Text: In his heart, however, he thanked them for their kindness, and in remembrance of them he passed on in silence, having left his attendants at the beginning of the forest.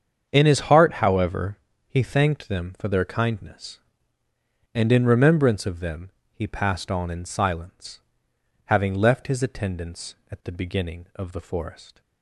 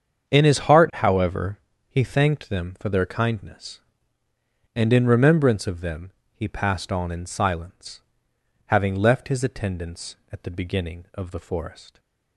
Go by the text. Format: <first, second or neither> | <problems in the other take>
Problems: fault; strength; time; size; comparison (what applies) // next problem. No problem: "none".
neither | starts louder than the rest; strong; the same in both // pauses between "them" and "he"; slight; the same in both